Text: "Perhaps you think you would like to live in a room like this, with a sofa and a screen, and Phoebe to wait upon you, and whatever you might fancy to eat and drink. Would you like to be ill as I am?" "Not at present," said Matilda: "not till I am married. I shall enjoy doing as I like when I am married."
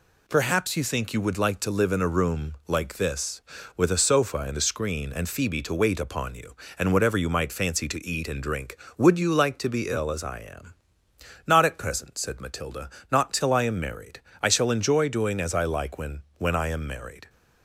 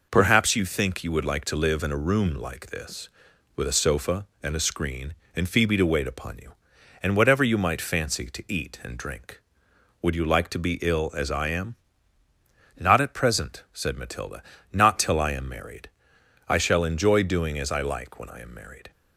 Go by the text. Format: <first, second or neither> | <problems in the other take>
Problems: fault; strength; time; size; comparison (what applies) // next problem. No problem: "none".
second | says "when" twice; at 16.3 s